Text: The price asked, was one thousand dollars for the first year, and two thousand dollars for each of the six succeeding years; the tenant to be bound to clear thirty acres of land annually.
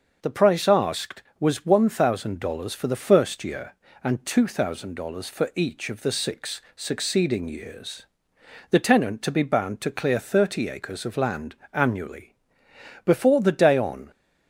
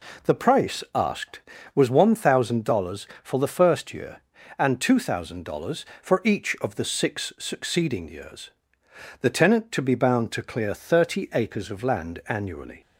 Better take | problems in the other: second | starts louder than the rest; until 1.2 s; 6.5 dB // pauses between "land" and "annually"; slight; at 11.5 s; 0.18 s long // goes on to say "Before the day on"; noticeable; from 13.0 s on; 1.0 s long

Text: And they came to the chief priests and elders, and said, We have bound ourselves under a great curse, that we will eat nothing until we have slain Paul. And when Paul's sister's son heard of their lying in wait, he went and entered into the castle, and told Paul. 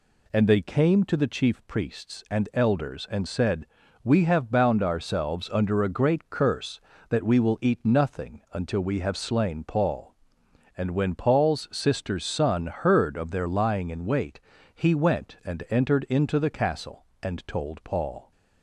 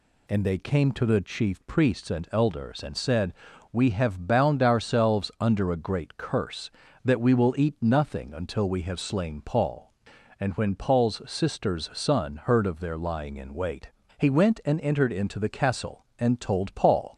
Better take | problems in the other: neither | none

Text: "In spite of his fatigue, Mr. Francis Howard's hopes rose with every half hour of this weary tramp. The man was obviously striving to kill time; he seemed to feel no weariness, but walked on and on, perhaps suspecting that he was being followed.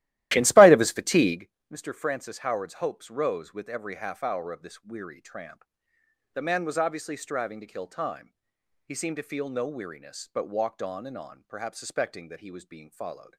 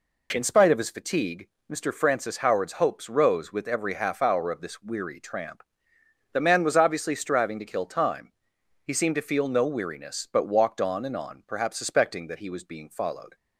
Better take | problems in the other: second | starts louder than the rest; strong; until 1.4 s; 15 dB

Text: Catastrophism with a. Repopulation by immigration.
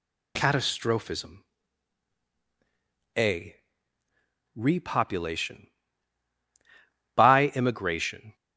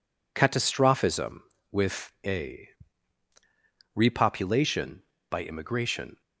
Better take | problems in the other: second | skips "with"; at 2.3 s

